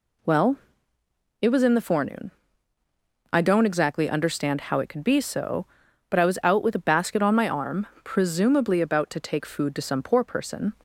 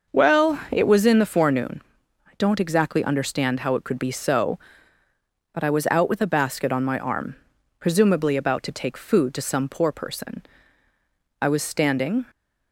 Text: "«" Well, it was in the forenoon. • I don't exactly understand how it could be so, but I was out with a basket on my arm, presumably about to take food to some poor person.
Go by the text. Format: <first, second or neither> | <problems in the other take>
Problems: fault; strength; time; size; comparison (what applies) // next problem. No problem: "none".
first | starts louder than the rest; noticeable; until 1.2 s; 6 dB // goes on to say "I was standing"; noticeable; from 11.4 s on; 0.84 s long